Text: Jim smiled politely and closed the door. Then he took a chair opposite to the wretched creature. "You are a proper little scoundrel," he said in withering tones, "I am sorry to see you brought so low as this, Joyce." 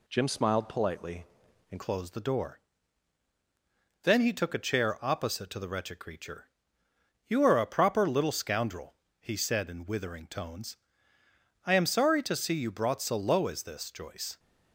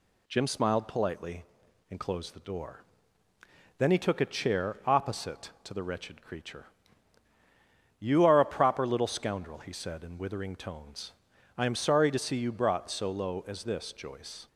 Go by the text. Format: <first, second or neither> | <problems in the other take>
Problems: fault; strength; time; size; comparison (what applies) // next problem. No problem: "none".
second | changes voice at "closed"; from 1.7 s on; 12.6 s long